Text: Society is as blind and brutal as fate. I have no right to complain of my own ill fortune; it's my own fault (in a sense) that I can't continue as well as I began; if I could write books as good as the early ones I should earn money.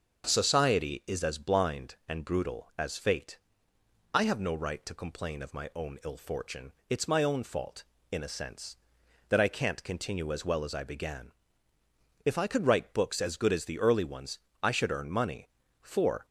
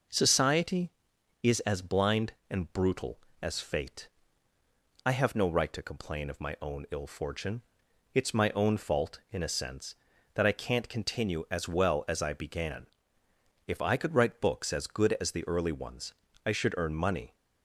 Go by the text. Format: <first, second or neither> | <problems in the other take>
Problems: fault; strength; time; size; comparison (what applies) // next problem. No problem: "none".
second | starts louder than the rest; until 1.2 s; 6.5 dB // pauses between "ones" and "I"; slight; at 14.3 s; 0.24 s long; slight in the second // goes on to say "For"; slight; from 15.8 s on; 0.42 s long